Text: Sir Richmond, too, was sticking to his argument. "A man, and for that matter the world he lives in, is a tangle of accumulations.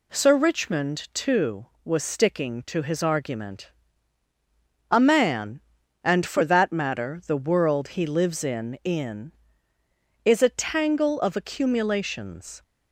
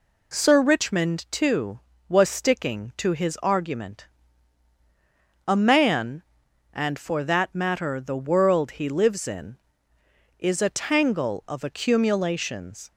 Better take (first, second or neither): second